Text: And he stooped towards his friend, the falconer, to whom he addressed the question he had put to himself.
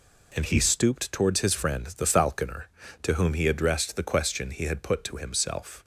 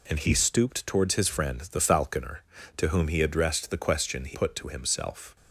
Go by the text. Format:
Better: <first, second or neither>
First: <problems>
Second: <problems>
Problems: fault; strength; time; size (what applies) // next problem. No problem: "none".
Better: first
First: none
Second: skips "had"; at 4.3 s